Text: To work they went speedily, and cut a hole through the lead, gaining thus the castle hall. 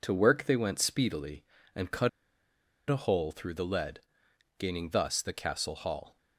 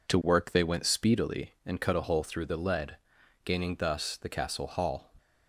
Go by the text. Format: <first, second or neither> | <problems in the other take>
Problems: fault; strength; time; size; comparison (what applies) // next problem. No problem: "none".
second | pauses between "cut" and "a"; noticeable; at 2.0 s; 0.81 s long